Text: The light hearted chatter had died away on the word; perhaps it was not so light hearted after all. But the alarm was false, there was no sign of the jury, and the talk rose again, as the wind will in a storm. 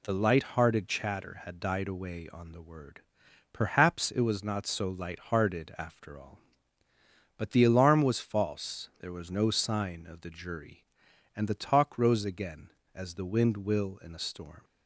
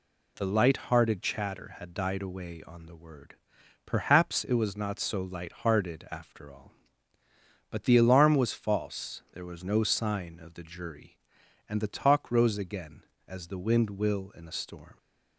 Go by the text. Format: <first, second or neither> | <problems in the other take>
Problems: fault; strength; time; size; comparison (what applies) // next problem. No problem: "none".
neither | none